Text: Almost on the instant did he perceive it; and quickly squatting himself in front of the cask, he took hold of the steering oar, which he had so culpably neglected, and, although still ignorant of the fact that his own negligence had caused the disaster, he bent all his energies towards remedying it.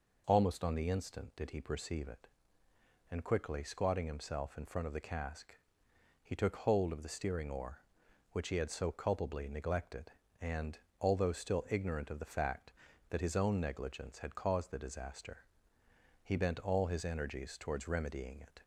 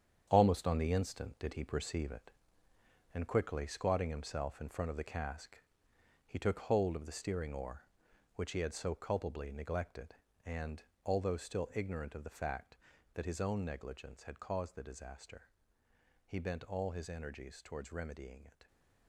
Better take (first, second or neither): first